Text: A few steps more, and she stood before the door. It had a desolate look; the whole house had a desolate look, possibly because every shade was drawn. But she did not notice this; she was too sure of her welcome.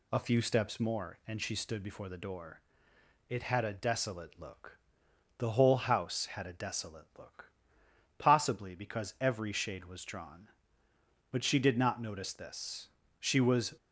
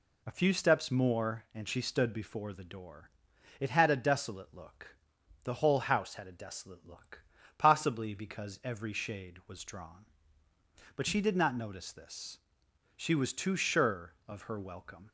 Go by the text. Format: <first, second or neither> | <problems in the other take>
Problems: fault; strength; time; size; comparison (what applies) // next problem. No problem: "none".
second | stops before "too sure of her welcome"; at 13.7 s